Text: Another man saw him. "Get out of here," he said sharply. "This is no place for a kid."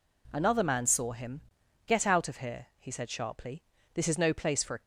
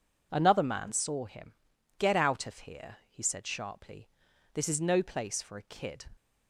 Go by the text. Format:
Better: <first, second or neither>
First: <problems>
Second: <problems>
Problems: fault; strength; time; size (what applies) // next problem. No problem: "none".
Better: second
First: stops before "kid"; at 4.8 s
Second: none